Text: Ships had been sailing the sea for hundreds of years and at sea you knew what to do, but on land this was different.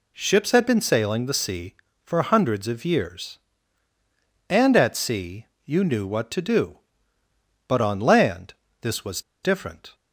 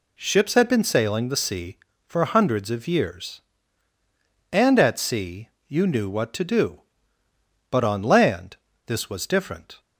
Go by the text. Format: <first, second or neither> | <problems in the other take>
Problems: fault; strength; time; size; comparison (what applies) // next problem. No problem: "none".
second | pauses between "sea" and "you"; slight; at 5.4 s; 0.18 s long; slight in the second // pauses between "land" and "this"; slight; at 8.5 s; 0.28 s long; slight in the second // pauses between "was" and "different"; slight; at 9.2 s; 0.22 s long